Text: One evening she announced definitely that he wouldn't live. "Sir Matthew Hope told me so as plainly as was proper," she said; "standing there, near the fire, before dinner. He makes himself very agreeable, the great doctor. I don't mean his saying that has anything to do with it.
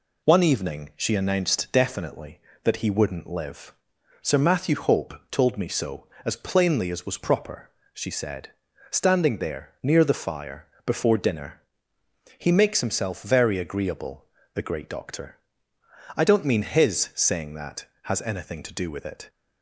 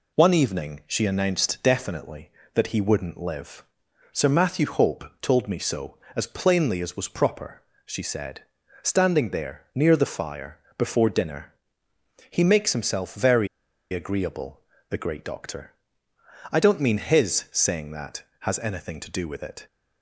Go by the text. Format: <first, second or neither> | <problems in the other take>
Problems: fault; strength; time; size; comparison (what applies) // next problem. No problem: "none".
first | pauses between "Hope" and "told"; slight; at 5.0 s; 0.18 s long; slight in the first // pauses between "very" and "agreeable"; at 13.4 s; 0.44 s long